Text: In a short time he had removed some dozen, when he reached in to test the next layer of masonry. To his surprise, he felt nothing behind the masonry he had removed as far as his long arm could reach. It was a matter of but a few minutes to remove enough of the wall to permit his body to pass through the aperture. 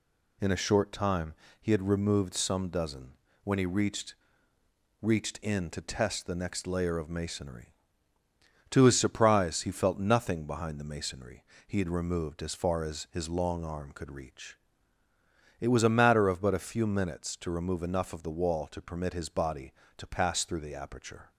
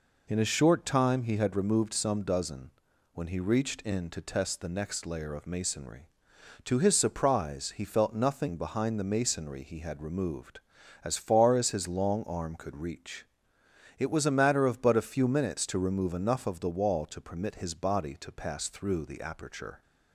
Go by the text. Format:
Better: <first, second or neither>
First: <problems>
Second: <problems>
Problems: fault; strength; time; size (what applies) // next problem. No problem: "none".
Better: second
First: pauses between "time" and "he"; slight; at 1.3 s; 0.28 s long // says "reached" twice; at 5.0 s // pauses between "masonry" and "he"; slight; at 11.4 s; 0.24 s long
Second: none